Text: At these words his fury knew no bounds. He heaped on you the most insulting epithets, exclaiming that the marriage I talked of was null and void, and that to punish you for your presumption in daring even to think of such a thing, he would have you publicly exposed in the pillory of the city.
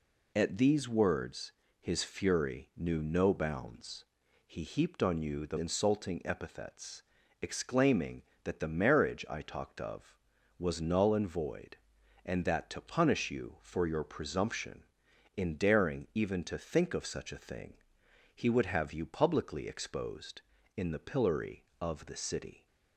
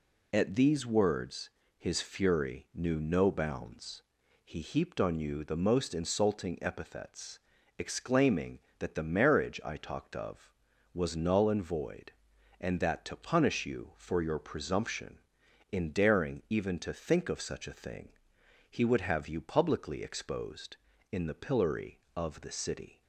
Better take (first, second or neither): second